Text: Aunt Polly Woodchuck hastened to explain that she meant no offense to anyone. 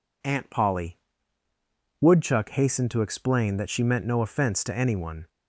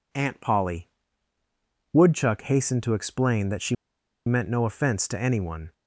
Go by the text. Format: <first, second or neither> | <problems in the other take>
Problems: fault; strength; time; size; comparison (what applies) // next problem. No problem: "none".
first | pauses between "Polly" and "Woodchuck"; at 0.8 s; 1.0 s long; also in the first // pauses between "she" and "meant"; noticeable; at 3.7 s; 0.51 s long